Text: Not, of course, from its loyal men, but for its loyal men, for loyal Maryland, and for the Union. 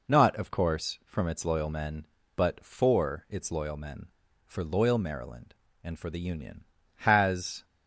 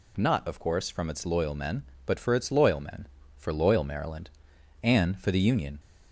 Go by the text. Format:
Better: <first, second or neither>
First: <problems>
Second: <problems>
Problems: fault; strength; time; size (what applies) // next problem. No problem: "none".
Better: second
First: goes on to say "Has"; noticeable; from 6.9 s on; 0.66 s long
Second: none